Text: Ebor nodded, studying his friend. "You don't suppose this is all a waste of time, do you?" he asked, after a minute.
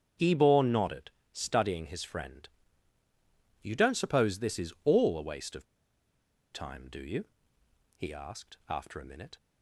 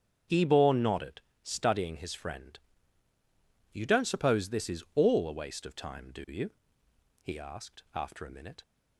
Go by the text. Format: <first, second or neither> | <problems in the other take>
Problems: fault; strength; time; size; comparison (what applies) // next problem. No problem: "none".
second | starts louder than the rest; strong; until 1.4 s; 7.5 dB; strong in the second // pauses between "of" and "time"; noticeable; at 5.6 s; 0.88 s long